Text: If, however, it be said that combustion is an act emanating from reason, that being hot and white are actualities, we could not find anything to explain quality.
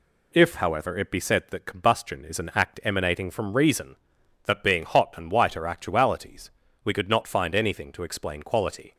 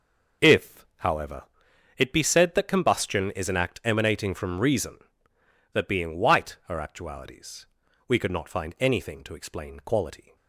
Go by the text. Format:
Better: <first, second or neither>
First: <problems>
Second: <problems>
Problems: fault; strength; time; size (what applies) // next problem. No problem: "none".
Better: first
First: none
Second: starts louder than the rest; noticeable; until 2.0 s; 6 dB // skips "hot and"; at 6.1 s